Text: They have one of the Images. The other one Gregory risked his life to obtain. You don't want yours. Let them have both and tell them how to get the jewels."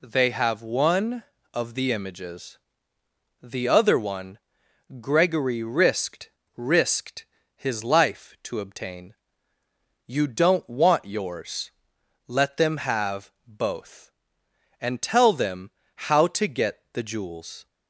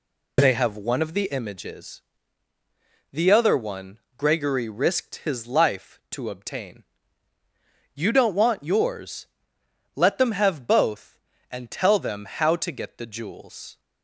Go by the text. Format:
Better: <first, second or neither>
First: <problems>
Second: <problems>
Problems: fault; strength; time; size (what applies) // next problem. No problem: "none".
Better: second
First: pauses between "one" and "Gregory"; noticeable; at 4.3 s; 0.62 s long // says "risked" twice; at 6.5 s // pauses between "have" and "both"; slight; at 13.3 s; 0.16 s long // pauses between "them" and "how"; slight; at 15.7 s; 0.24 s long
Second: pauses between "one" and "Gregory"; slight; at 3.9 s; 0.18 s long